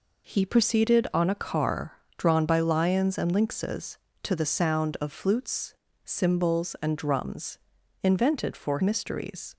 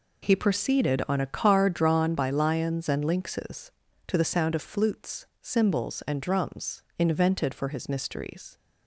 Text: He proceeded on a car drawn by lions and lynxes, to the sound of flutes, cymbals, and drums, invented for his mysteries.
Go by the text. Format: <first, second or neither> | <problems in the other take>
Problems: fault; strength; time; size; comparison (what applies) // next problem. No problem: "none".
second | pauses between "car" and "drawn"; slight; at 1.9 s; 0.18 s long // skips "his"; at 8.8 s